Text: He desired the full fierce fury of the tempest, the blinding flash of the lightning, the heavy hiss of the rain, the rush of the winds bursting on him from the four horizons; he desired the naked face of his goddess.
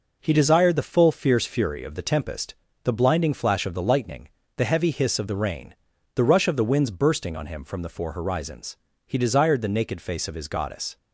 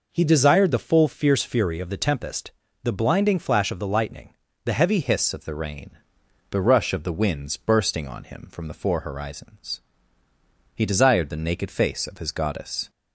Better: first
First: none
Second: changes voice at "hiss"; from 5.0 s on; 7.8 s long

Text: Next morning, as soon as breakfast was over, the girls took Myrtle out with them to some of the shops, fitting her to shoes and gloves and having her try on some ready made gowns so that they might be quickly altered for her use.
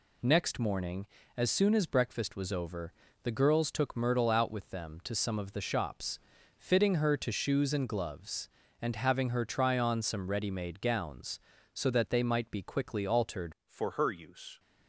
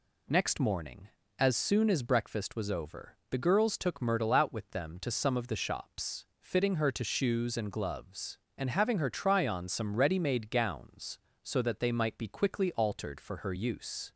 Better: second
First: changes voice at "for"; from 13.6 s on; 0.9 s long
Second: none

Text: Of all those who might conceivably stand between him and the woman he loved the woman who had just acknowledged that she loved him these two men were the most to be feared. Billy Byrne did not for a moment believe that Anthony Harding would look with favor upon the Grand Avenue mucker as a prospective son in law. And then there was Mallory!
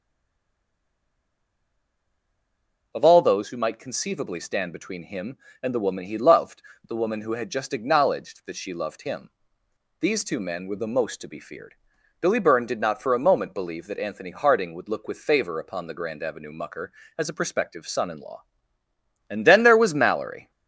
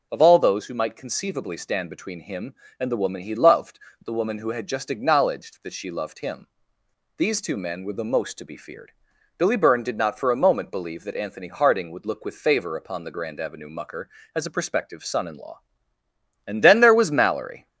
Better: second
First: stays silent before the first word; strong; until 2.9 s; 2.9 s long // pauses between "loved" and "the"; slight; at 6.6 s; 0.26 s long // pauses between "him" and "these"; noticeable; at 9.3 s; 0.68 s long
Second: pauses between "loved" and "the"; slight; at 3.7 s; 0.26 s long // pauses between "him" and "these"; noticeable; at 6.4 s; 0.68 s long

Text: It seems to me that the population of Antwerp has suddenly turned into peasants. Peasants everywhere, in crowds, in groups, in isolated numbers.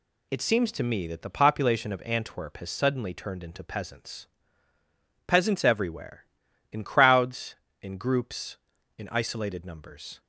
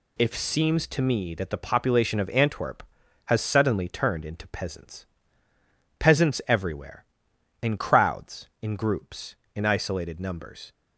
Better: first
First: none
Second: says "If" for "It"; at 0.1 s

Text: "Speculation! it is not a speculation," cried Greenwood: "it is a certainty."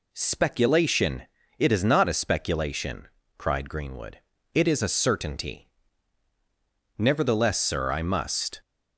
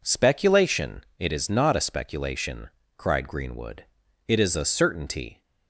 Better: second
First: goes on to say "Nevertheless sir I must"; from 6.9 s on; 1.6 s long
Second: none

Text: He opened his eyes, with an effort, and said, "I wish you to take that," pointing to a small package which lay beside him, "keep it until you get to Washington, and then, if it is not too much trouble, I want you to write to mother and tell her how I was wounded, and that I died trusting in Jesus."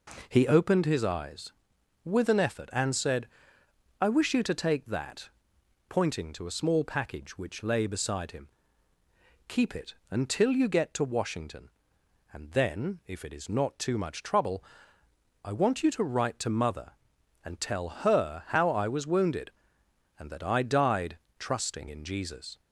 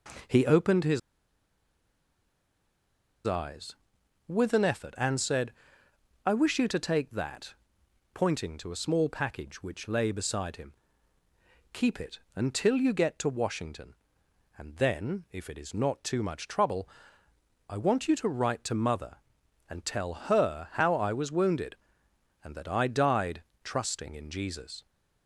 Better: first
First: pauses between "died" and "trusting"; slight; at 21.1 s; 0.18 s long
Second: pauses between "his" and "eyes"; strong; at 0.9 s; 2.2 s long // pauses between "died" and "trusting"; slight; at 23.4 s; 0.18 s long

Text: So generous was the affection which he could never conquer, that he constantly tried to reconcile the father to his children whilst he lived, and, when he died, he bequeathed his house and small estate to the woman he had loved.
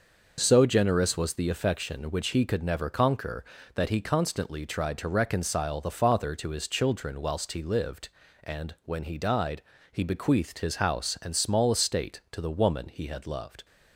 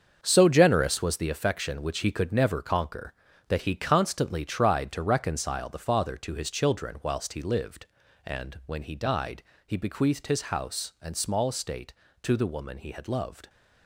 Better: first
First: none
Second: gets quieter; strong; throughout; 10 dB

